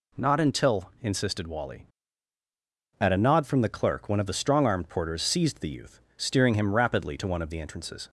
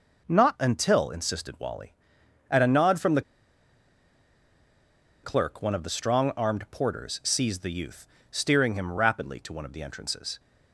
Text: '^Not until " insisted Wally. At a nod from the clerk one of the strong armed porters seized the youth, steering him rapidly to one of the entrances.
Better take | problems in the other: first | pauses between "the" and "clerk"; strong; at 3.2 s; 2.0 s long

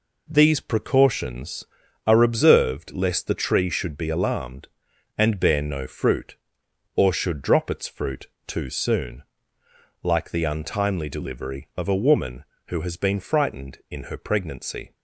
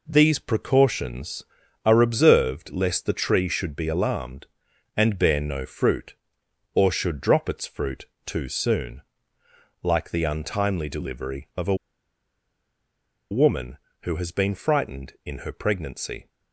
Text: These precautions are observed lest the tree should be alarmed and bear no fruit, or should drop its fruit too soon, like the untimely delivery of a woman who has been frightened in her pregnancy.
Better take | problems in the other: first | pauses between "fruit" and "too"; slight; at 8.0 s; 0.18 s long; slight in the first // pauses between "a" and "woman"; strong; at 11.7 s; 1.5 s long

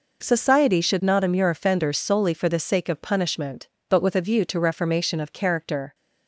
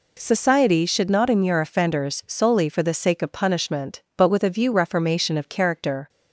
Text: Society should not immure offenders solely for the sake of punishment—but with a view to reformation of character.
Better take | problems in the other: first | skips "to"; at 4.7 s

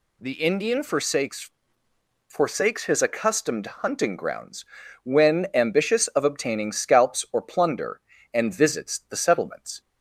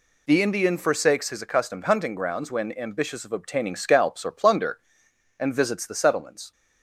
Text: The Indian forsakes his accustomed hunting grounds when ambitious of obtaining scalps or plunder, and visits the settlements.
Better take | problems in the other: second | says "forsakes" twice; at 2.2 s // pauses between "grounds" and "when"; at 4.6 s; 0.38 s long

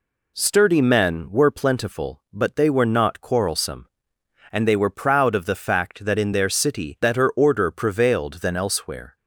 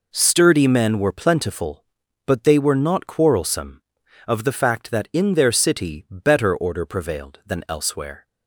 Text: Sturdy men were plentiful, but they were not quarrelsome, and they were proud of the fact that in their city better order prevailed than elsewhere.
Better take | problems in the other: first | skips "and they were proud"; at 4.0 s

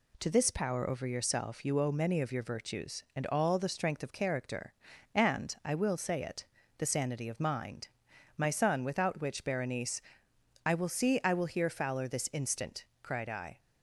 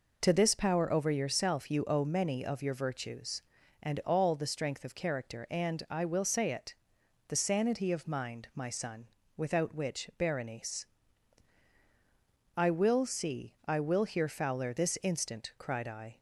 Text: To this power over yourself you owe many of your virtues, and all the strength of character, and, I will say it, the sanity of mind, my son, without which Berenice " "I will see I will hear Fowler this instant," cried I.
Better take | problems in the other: neither | none

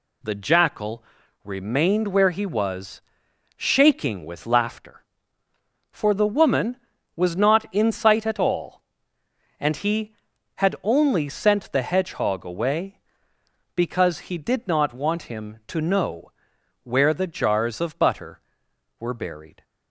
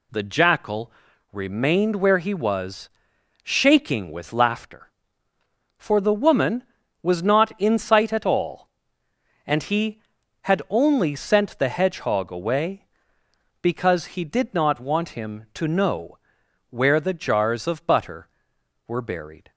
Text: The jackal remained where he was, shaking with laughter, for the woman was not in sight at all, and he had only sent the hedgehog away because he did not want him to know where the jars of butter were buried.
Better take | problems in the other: neither | pauses between "jackal" and "remained"; the same in both // pauses between "know" and "where"; noticeable; the same in both

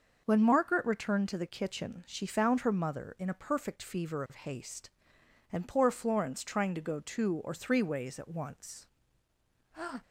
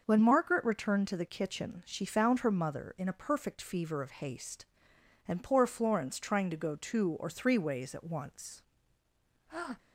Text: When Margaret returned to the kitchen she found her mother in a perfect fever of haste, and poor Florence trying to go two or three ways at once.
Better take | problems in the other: neither | starts louder than the rest; the same in both

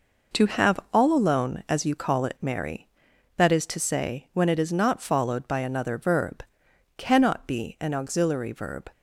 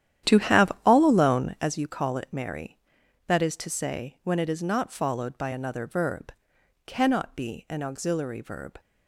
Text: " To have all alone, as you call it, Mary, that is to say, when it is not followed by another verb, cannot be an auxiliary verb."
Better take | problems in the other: first | starts louder than the rest; strong; until 1.7 s; 11 dB

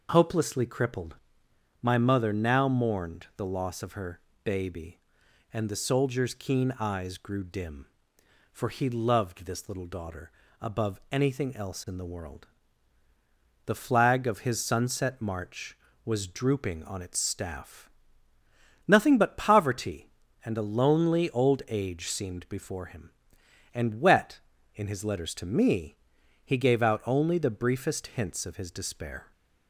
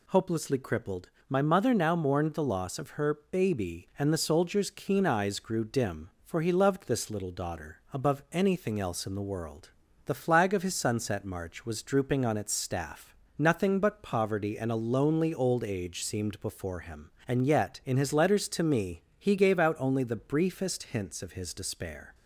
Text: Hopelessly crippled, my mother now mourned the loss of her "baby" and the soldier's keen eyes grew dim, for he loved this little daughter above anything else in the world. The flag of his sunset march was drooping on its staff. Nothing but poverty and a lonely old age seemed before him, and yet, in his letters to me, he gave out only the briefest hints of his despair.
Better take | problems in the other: second | pauses between "her" and "baby"; slight; at 4.1 s; 0.24 s long // pauses between "daughter" and "above"; slight; at 10.3 s; 0.28 s long // says "wet" for "yet"; at 23.9 s

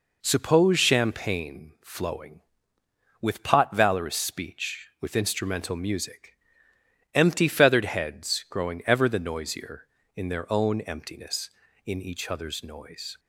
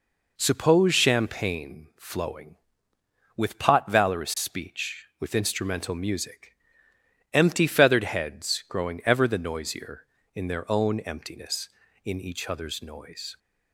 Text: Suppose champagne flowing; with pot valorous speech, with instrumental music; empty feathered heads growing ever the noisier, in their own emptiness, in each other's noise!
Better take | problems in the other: neither | none

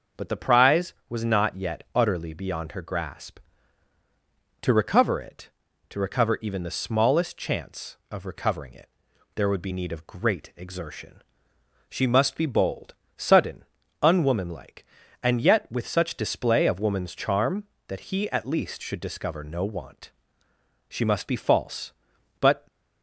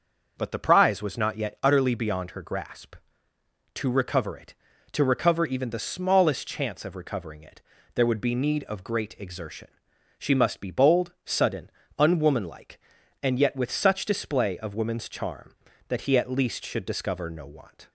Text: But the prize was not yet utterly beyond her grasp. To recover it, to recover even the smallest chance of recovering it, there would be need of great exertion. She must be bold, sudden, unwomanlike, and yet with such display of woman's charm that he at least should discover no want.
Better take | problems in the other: second | goes on to say "She must be false but"; strong; from 20.8 s on; 1.7 s long

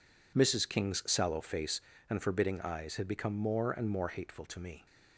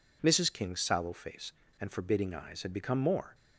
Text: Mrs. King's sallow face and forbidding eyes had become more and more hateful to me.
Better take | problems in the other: first | stops before "and more hateful to me"; at 3.3 s

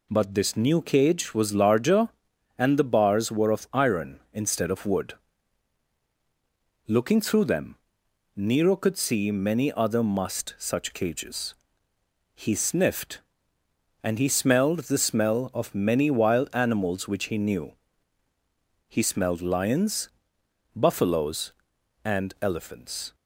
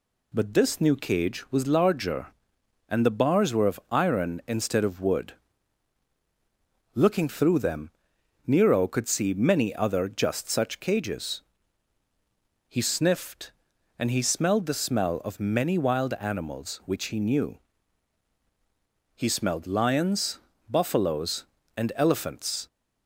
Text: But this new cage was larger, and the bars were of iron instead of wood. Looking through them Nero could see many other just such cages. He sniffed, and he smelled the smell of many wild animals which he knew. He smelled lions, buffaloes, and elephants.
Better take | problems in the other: second | pauses between "them" and "Nero"; noticeable; at 7.7 s; 0.60 s long; noticeable in the second // says "must" for "just"; at 10.0 s

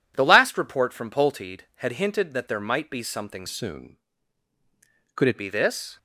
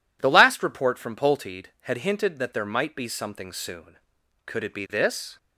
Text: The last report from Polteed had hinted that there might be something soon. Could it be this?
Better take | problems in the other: second | changes voice from "soon" to "it"; from 3.4 to 5.3 s; 1.9 s long

